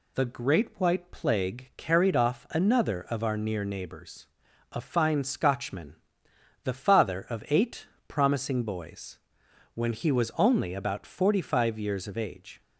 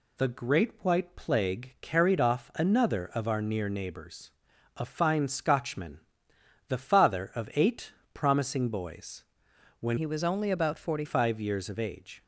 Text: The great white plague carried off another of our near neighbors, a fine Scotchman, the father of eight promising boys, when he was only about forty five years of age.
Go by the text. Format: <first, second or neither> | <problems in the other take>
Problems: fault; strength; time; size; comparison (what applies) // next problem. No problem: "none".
first | pauses between "eight" and "promising"; slight; at 7.9 s; 0.20 s long; slight in the first // changes voice from "he" to "forty"; from 9.9 to 11.0 s; 1.1 s long